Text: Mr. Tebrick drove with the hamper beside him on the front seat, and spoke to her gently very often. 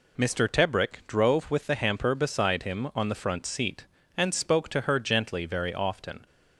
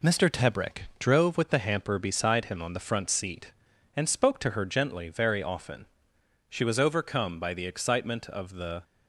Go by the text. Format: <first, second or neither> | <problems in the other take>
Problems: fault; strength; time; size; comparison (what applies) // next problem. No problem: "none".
first | goes on to say "She was overcome by the excitement of the"; strong; from 6.4 s on; 2.3 s long